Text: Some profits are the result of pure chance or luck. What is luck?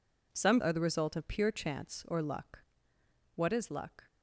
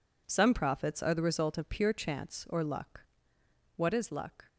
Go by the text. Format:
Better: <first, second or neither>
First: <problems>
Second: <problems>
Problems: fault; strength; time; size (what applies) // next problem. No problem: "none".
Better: second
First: skips "profits"; at 0.6 s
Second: none